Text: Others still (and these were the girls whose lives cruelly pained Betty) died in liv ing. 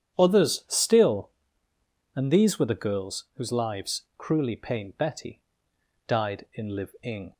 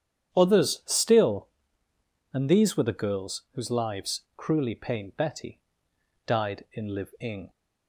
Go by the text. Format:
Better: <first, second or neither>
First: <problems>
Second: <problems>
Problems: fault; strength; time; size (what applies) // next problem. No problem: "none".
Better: neither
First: starts louder than the rest; strong; until 1.2 s; 9 dB // pauses between "lives" and "cruelly"; slight; at 4.0 s; 0.16 s long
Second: starts louder than the rest; strong; until 1.3 s; 9 dB // pauses between "lives" and "cruelly"; slight; at 4.2 s; 0.16 s long